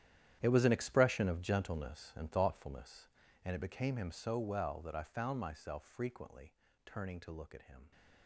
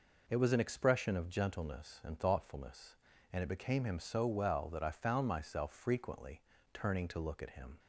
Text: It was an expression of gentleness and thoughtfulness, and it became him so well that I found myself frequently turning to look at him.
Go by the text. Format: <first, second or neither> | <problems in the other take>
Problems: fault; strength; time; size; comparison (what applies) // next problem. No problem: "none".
second | gets quieter; strong; throughout; 15.5 dB // pauses between "frequently" and "turning"; slight; at 6.5 s; 0.32 s long; slight in the second